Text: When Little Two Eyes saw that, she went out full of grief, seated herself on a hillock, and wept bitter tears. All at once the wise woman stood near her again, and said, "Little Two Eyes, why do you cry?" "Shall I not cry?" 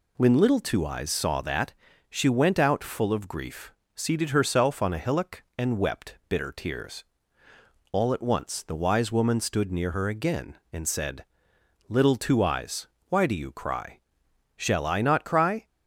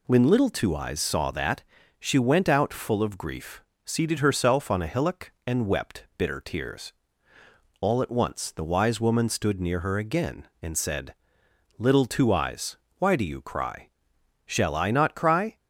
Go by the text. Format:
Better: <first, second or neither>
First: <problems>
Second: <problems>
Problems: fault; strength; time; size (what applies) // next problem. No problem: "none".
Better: neither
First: none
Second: none